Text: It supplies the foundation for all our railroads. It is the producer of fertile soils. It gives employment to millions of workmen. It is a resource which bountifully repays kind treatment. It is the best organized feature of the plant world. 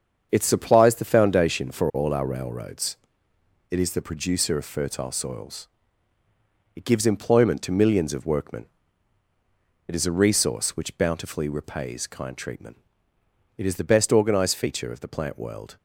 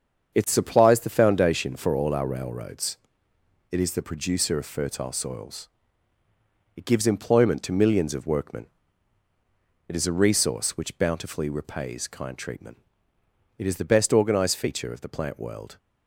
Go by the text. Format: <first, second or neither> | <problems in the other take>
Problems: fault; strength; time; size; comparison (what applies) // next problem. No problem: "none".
neither | starts louder than the rest; strong; the same in both